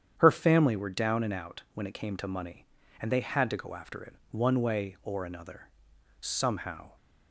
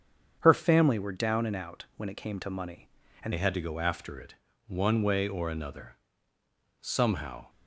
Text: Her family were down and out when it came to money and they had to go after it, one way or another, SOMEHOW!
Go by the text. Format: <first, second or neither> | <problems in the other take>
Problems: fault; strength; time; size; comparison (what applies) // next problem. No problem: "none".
first | starts louder than the rest; strong; until 1.4 s; 7.5 dB; strong in the first // changes voice at "they"; from 3.3 s on; 4.1 s long